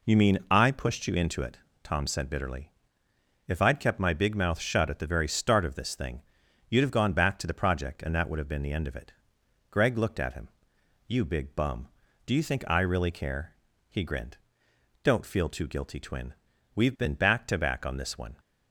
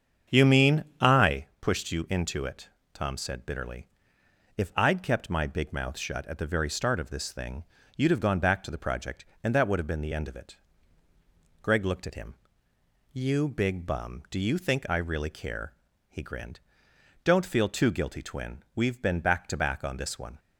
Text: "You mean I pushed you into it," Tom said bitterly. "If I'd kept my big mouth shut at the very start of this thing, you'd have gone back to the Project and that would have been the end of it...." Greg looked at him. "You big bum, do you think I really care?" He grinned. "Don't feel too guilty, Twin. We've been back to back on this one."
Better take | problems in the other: first | starts louder than the rest; strong; until 1.5 s; 7.5 dB // pauses between "mean" and "I"; slight; at 0.8 s; 0.16 s long // pauses between "I" and "pushed"; slight; at 1.4 s; 0.16 s long

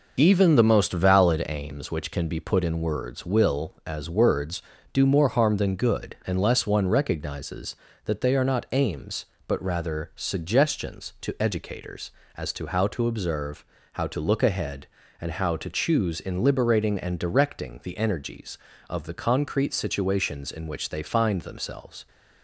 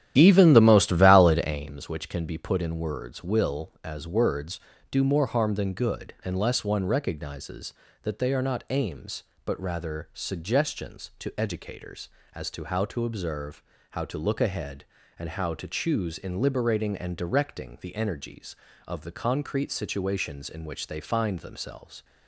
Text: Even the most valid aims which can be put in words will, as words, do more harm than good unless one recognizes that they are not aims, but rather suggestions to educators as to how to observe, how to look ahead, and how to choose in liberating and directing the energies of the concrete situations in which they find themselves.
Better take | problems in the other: first | starts louder than the rest; strong; until 1.7 s; 11.5 dB

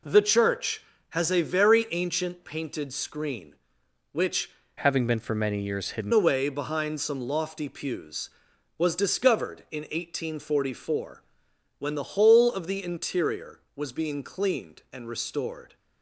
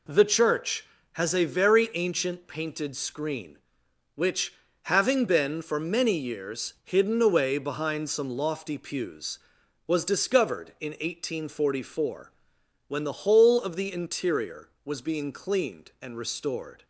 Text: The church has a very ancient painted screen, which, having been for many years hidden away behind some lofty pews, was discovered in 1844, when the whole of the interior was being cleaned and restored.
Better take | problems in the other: second | changes voice from "having" to "hidden"; from 4.8 to 6.1 s; 1.3 s long

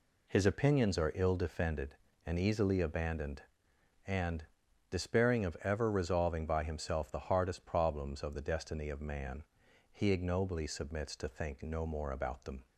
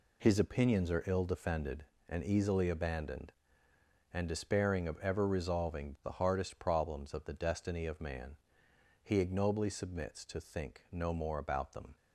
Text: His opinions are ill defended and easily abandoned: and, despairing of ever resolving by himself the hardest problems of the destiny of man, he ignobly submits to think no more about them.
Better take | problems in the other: first | skips "by himself"; at 5.9 s

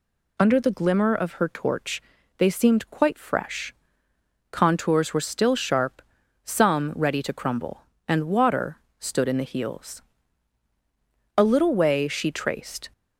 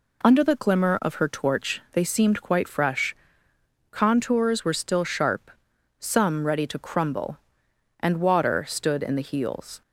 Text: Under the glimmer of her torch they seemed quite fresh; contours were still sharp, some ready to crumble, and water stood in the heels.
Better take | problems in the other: second | pauses between "torch" and "they"; slight; at 2.0 s; 0.36 s long // pauses between "water" and "stood"; slight; at 8.7 s; 0.22 s long // goes on to say "A little way she traced"; from 11.3 s on; 1.5 s long

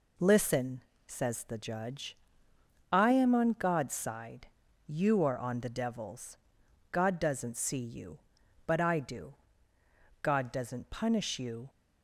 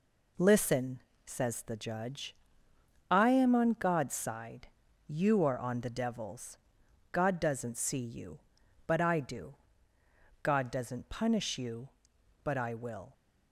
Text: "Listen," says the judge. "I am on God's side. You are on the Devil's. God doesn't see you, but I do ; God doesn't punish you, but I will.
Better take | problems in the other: second | stops before "but I will"; at 11.6 s

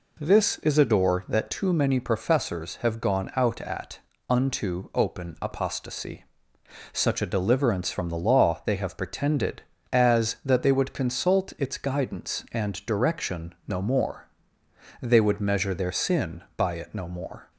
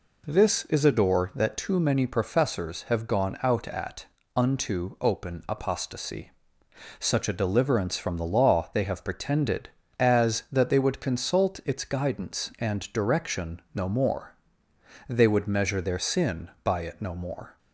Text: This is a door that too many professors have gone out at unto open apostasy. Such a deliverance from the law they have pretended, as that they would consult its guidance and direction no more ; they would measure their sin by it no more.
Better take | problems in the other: neither | pauses between "at" and "unto"; slight; the same in both

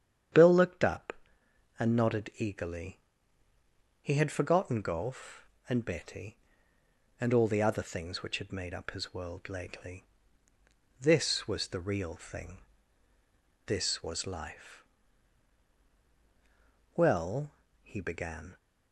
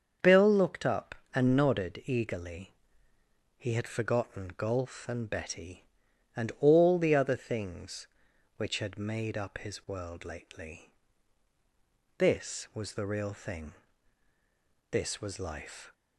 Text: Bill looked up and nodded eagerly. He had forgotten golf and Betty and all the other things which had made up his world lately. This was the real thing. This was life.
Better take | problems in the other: second | starts louder than the rest; strong; until 1.9 s; 9 dB; also in the second // goes on to say "Well he began"; from 16.9 s on; 1.6 s long

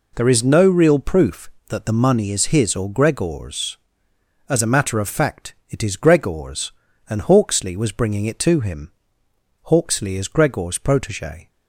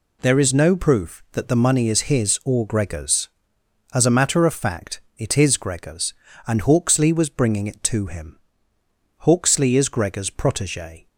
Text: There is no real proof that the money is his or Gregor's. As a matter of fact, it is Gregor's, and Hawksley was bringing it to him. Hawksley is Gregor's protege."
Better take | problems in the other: first | skips "real"; at 0.7 s

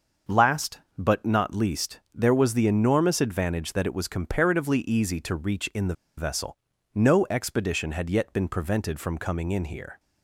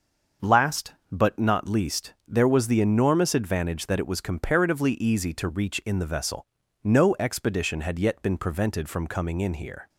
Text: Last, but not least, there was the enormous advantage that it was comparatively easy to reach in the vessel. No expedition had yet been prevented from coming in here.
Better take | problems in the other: second | starts louder than the rest; until 1.4 s; 6.5 dB; also in the second // pauses between "the" and "vessel"; slight; at 5.9 s; 0.24 s long

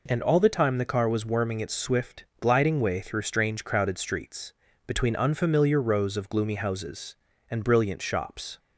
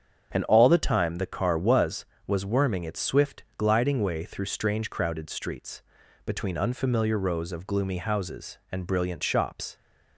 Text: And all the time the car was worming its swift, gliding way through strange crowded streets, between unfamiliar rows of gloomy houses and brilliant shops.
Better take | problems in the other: first | starts louder than the rest; strong; until 1.3 s; 7.5 dB // says "was" twice; at 2.2 s

